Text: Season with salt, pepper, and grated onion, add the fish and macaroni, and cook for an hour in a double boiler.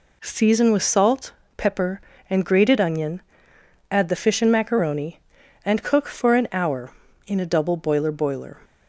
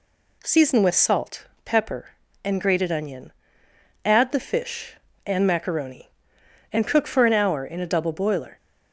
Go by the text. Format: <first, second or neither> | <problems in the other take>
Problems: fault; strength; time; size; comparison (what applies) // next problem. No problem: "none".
second | says "boiler" twice; at 8.1 s